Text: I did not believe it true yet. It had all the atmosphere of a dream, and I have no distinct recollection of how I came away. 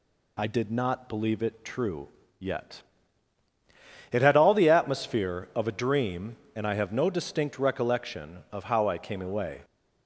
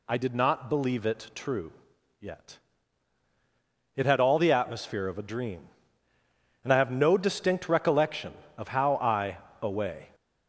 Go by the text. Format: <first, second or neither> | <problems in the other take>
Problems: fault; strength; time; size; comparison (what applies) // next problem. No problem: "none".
first | pauses between "true" and "yet"; noticeable; at 1.7 s; 0.48 s long; slight in the first // skips "came"; at 9.4 s